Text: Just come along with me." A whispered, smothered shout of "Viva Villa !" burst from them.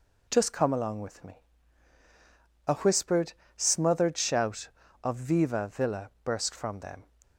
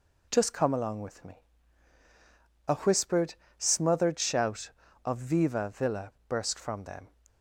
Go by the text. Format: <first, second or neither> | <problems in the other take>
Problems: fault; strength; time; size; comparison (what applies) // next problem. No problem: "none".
neither | none